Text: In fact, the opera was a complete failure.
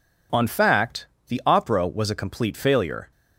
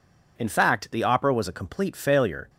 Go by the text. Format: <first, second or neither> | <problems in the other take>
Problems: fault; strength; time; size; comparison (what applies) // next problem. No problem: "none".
second | says "On" for "In"; at 0.3 s